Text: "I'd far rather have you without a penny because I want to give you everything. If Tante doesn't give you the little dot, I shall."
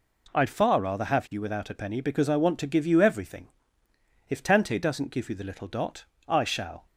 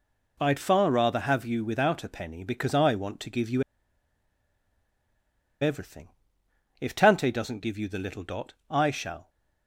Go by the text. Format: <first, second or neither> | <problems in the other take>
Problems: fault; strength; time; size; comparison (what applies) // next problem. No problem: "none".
first | pauses between "you" and "everything"; strong; at 3.6 s; 1.9 s long